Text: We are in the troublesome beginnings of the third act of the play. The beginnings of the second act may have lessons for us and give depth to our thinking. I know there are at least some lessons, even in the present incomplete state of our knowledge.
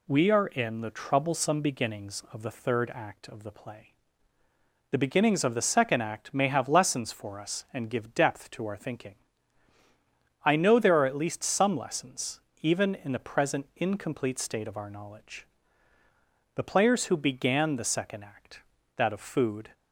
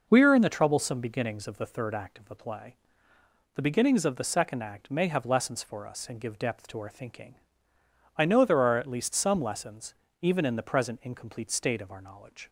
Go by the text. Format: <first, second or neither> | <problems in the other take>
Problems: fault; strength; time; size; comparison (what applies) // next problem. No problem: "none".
second | goes on to say "The players who began the second act that of food"; strong; from 16.5 s on; 3.1 s long